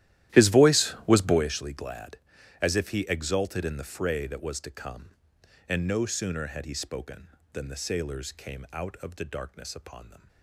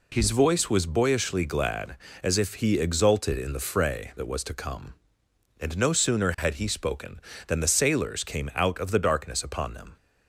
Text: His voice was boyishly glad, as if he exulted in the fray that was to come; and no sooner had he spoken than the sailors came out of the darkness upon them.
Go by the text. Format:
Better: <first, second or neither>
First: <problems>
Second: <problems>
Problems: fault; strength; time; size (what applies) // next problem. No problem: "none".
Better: second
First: starts louder than the rest; strong; until 1.5 s; 13.5 dB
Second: none